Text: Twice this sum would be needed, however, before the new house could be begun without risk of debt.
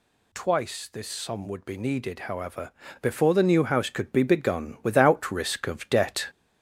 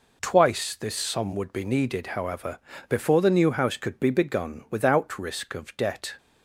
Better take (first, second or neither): second